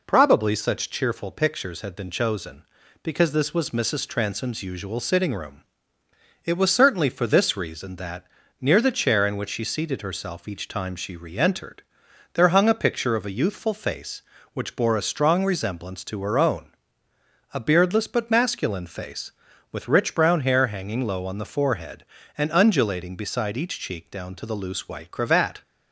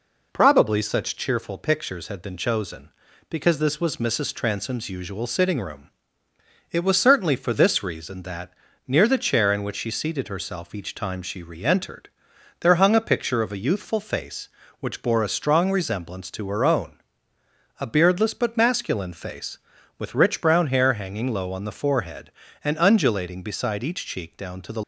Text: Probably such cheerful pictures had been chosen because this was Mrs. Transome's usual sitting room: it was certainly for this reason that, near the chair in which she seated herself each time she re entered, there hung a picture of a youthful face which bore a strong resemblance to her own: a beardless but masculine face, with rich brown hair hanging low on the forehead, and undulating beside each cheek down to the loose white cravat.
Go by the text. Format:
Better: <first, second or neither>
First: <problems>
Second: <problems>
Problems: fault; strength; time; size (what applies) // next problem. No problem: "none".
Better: first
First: none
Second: stops before "loose white cravat"; at 24.8 s